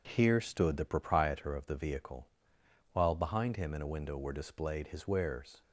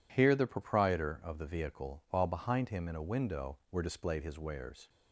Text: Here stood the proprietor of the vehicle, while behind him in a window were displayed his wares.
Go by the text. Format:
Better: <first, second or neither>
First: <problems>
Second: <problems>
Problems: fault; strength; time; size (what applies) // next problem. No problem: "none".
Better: first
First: none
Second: skips "stood"; at 0.3 s